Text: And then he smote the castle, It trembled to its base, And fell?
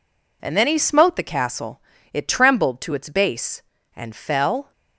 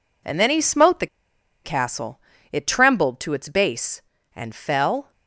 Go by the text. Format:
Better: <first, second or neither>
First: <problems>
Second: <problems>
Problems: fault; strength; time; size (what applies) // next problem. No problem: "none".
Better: first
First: none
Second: pauses between "the" and "castle"; noticeable; at 1.0 s; 0.58 s long